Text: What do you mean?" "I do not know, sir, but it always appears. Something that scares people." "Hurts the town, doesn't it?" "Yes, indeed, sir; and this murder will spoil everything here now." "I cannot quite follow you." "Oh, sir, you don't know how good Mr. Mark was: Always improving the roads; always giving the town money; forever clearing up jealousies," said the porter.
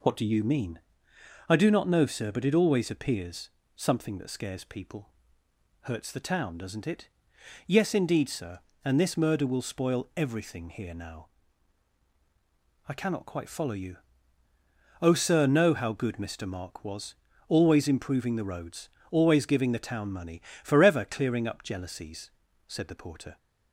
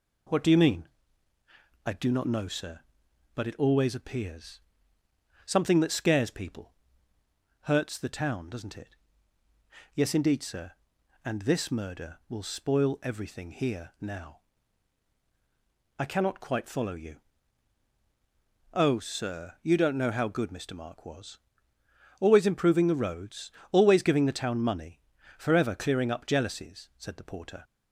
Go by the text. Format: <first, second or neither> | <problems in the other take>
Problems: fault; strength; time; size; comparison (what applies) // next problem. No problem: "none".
second | skips "you don't"; at 15.4 s